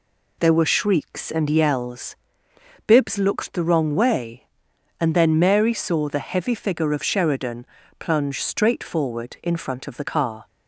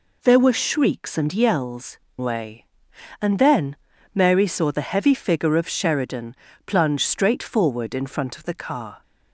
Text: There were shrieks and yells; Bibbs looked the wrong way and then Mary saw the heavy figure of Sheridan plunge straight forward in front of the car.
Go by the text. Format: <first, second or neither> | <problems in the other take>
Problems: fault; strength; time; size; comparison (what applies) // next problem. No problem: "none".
first | skips "Bibbs looked the wrong"; at 2.0 s // pauses between "then" and "Mary"; at 3.7 s; 0.38 s long // pauses between "Sheridan" and "plunge"; slight; at 6.3 s; 0.30 s long; slight in the first